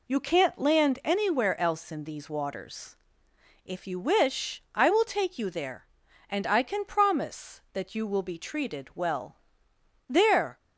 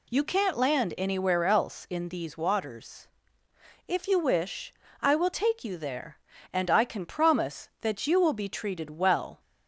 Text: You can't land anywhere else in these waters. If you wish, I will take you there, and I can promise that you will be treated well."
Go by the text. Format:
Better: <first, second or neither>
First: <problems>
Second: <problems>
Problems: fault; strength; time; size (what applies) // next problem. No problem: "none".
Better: second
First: goes on to say "There"; from 10.0 s on; 0.52 s long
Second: none